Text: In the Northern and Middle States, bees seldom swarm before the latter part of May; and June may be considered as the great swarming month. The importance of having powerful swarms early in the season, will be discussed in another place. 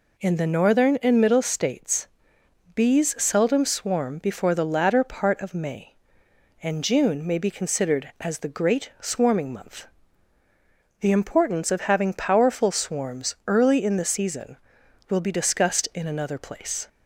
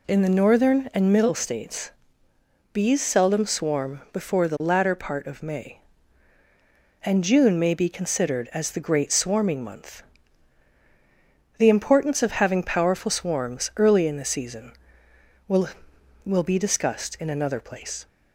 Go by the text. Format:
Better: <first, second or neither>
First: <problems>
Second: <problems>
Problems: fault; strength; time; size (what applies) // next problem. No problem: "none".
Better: first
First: none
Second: says "will" twice; at 16.2 s